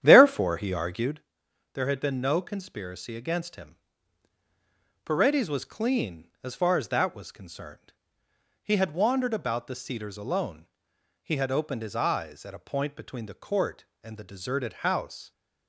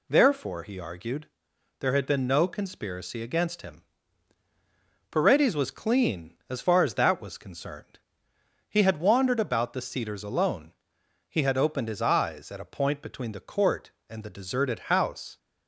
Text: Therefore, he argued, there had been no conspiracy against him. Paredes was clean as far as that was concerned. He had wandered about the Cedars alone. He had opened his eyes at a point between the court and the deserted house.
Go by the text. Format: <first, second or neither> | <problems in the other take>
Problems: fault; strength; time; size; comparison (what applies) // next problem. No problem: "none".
second | starts louder than the rest; strong; until 1.2 s; 10 dB